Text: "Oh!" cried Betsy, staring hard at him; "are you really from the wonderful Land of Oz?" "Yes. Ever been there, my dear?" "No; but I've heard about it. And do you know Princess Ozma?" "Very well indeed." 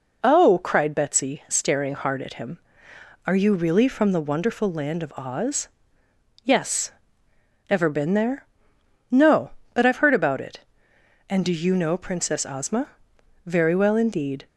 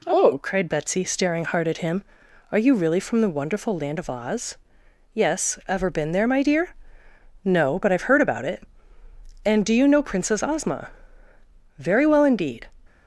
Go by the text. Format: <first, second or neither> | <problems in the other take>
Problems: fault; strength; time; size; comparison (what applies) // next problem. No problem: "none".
second | skips "my dear"; at 8.7 s